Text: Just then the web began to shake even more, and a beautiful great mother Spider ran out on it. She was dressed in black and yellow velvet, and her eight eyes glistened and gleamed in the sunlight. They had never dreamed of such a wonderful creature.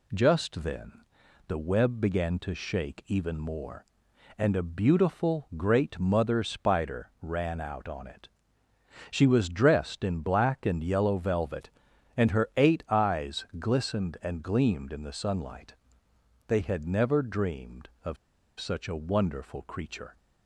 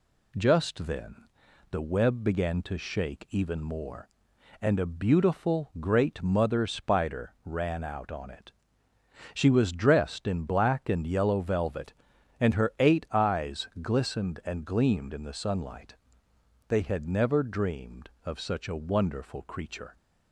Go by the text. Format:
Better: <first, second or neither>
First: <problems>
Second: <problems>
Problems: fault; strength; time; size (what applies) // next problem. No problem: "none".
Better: second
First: pauses between "then" and "the"; noticeable; at 1.0 s; 0.46 s long // pauses between "of" and "such"; at 18.1 s; 0.43 s long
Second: pauses between "then" and "the"; noticeable; at 1.2 s; 0.46 s long